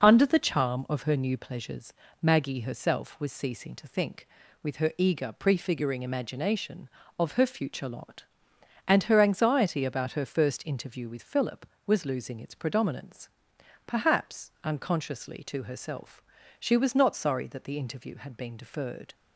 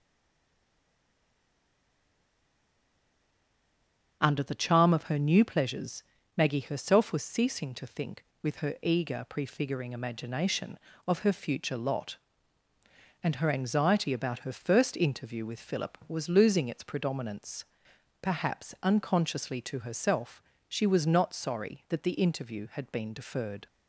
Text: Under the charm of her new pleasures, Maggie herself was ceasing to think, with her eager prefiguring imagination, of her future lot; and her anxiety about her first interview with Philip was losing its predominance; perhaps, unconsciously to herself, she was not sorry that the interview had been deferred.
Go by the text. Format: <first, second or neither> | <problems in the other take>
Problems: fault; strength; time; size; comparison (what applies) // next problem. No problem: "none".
first | stays silent before the first word; strong; until 4.2 s; 4.2 s long // starts louder than the rest; until 5.2 s; 7 dB